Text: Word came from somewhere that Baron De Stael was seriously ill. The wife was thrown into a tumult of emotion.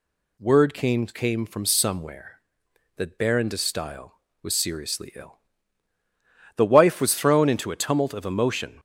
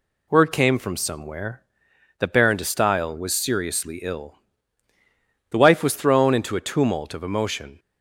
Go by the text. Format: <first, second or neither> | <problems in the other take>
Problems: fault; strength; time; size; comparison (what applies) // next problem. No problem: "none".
second | says "came" twice; at 1.0 s